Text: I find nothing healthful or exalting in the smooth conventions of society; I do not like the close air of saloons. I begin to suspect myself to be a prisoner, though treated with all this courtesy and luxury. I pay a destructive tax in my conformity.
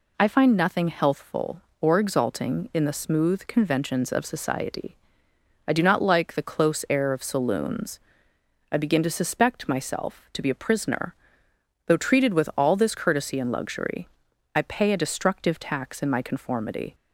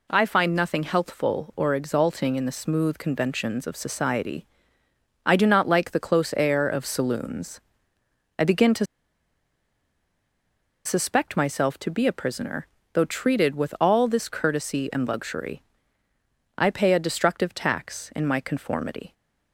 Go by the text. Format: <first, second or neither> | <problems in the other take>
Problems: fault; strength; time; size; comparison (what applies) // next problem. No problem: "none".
first | pauses between "to" and "suspect"; strong; at 8.8 s; 1.9 s long